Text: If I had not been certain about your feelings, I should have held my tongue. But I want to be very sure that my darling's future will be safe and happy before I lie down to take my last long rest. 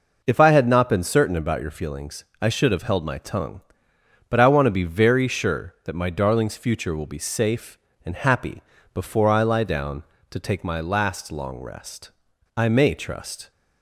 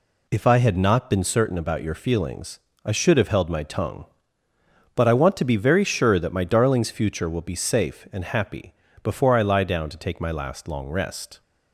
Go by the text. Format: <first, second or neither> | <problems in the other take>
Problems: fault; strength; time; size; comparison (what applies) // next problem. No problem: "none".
second | pauses between "happy" and "before"; slight; at 8.6 s; 0.32 s long; slight in the second // goes on to say "I may trust"; noticeable; from 12.5 s on; 0.94 s long